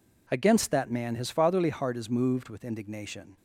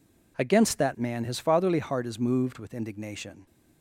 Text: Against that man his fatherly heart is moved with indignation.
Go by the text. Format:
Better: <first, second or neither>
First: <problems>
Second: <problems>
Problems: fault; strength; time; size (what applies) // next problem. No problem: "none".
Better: neither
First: none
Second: none